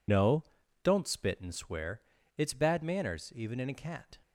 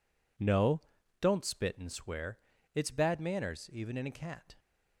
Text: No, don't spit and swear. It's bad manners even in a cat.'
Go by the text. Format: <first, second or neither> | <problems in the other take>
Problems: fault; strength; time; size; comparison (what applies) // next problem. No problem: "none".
second | loses the start of "No"; at 0.0 s; 70 ms